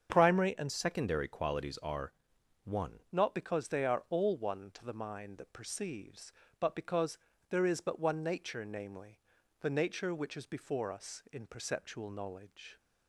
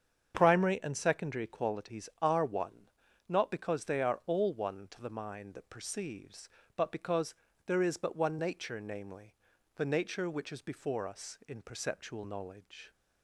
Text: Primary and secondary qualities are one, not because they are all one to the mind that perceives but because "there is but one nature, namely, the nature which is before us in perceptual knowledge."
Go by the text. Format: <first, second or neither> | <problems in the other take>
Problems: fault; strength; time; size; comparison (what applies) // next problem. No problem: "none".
second | starts louder than the rest; strong; until 1.1 s; 7 dB; strong in the second // changes voice from "secondary" to "one"; from 0.7 to 3.0 s; 2.3 s long // pauses between "are" and "one"; noticeable; at 2.1 s; 0.50 s long // pauses between "because" and "there"; slight; at 7.1 s; 0.34 s long; slight in the second